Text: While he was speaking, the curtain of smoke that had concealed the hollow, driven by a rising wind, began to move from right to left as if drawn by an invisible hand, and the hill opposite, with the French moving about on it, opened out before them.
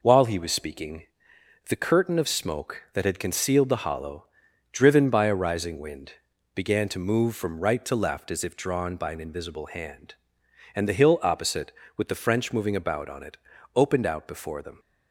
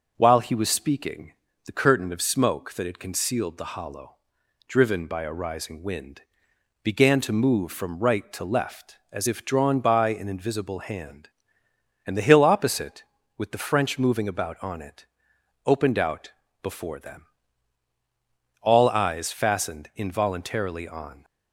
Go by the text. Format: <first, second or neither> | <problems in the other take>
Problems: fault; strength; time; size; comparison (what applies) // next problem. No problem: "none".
first | pauses between "out" and "before"; slight; at 16.3 s; 0.28 s long // goes on to say "All eyes fastened involuntarily on"; strong; from 18.6 s on; 2.6 s long